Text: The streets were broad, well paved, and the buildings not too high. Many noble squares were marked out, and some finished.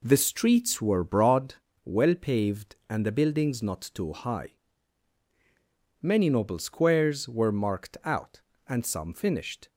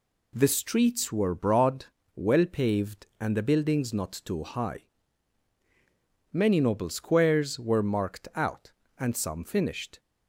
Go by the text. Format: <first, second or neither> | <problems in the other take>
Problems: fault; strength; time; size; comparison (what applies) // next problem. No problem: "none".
second | starts louder than the rest; slight; until 1.4 s; 3.5 dB